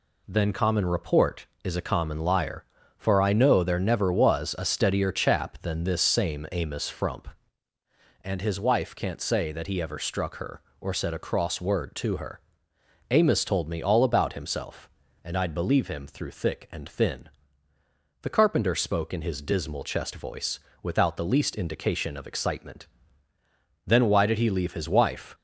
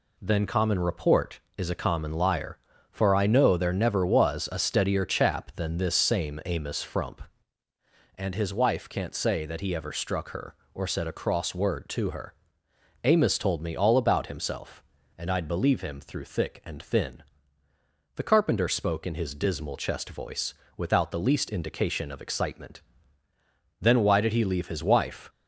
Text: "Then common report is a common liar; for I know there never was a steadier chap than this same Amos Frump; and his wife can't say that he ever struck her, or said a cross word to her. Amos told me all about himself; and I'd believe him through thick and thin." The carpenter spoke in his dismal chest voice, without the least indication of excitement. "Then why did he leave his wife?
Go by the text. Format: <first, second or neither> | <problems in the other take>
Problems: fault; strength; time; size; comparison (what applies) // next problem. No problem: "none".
neither | none